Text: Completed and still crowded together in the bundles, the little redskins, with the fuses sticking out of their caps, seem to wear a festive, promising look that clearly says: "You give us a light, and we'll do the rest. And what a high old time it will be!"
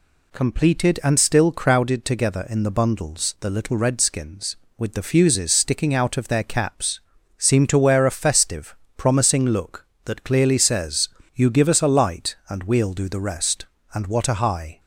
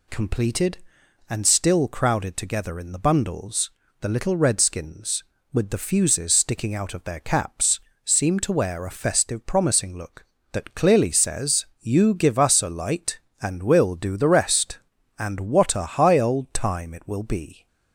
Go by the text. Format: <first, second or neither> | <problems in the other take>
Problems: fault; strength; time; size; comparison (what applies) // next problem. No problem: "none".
second | stops before "old time it will be"; at 14.7 s